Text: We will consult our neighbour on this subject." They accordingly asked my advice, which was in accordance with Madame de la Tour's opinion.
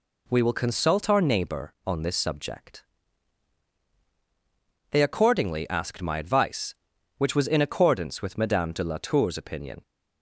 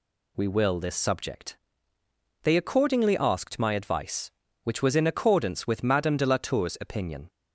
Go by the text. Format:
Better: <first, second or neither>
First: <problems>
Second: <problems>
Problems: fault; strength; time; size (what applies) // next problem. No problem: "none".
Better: first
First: none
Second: skips "consult our neighbour on"; at 0.8 s